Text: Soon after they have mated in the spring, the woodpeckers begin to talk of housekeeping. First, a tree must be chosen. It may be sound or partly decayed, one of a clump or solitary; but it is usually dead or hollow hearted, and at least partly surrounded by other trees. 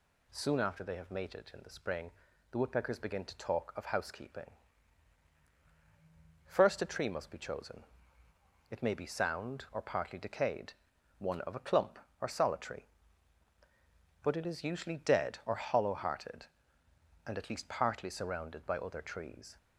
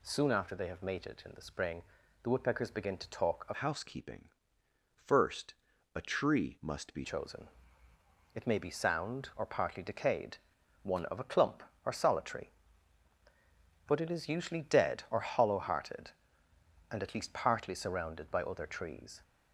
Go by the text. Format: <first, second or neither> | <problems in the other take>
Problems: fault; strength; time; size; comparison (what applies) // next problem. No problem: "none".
first | changes voice from "housekeeping" to "be"; from 3.5 to 7.0 s; 3.5 s long